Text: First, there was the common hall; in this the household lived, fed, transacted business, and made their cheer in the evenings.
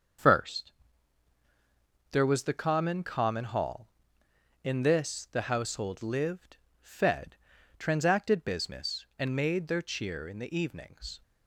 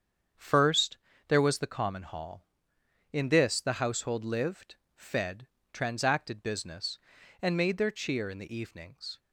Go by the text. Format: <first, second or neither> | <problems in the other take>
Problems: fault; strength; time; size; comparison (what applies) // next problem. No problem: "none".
second | starts louder than the rest; until 2.5 s; 6.5 dB; strong in the second // says "common" twice; at 3.0 s